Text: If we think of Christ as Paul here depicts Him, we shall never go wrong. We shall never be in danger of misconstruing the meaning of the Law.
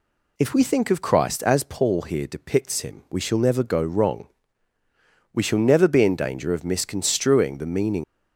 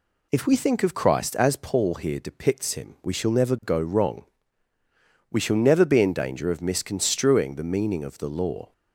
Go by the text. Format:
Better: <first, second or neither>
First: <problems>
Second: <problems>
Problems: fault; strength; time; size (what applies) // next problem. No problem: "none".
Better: second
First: stops before "of the Law"; at 8.0 s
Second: none